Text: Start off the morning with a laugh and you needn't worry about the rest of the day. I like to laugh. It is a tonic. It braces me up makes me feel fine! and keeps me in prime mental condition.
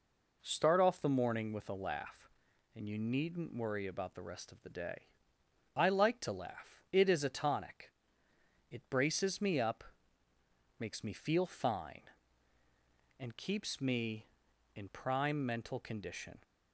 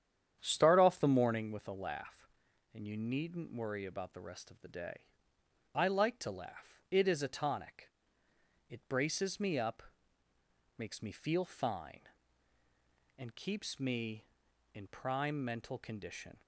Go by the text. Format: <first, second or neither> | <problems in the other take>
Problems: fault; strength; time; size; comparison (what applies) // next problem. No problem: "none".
first | starts louder than the rest; strong; until 1.5 s; 9 dB // pauses between "up" and "makes"; noticeable; at 9.8 s; 0.96 s long; noticeable in the first